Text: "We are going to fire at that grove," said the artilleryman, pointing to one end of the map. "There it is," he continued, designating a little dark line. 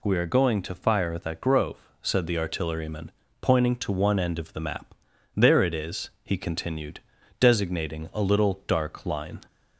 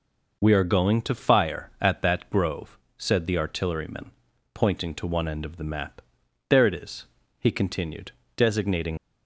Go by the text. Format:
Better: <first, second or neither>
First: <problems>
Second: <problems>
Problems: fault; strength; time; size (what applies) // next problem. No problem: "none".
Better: first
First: none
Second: stops before "a little dark line"; at 8.9 s